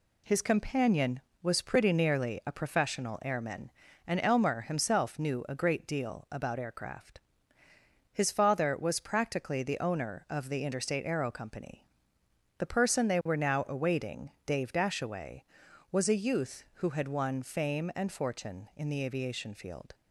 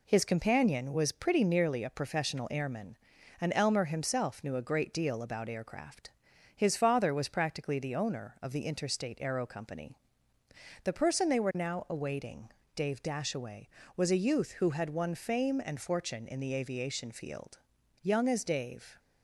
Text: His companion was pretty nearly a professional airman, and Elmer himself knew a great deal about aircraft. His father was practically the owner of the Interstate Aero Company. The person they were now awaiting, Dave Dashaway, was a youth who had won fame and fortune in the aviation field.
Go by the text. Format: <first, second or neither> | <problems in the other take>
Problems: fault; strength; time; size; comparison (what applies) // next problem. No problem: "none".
first | goes on to say "Young as Dave"; noticeable; from 18.0 s on; 0.96 s long